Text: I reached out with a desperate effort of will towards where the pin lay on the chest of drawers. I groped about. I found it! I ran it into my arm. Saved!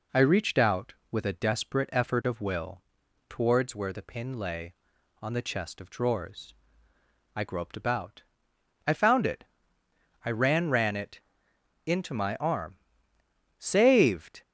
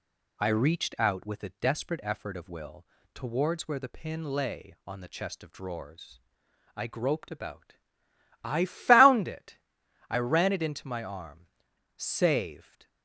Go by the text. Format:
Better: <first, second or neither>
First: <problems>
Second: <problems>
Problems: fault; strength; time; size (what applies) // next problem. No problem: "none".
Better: second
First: pauses between "will" and "towards"; noticeable; at 2.8 s; 0.48 s long // says "ran" twice; at 10.6 s // pauses between "it" and "into"; noticeable; at 11.1 s; 0.66 s long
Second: pauses between "will" and "towards"; slight; at 2.8 s; 0.28 s long